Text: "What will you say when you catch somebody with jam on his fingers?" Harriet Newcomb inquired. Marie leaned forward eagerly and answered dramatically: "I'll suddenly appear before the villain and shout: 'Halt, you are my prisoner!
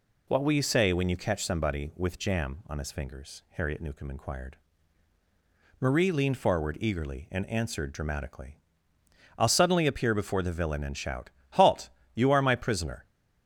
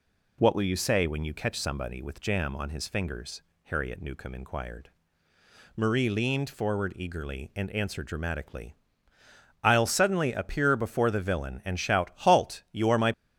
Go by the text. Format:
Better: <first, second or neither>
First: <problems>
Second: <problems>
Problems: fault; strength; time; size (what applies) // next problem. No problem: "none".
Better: first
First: none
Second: stops before "prisoner"; at 13.1 s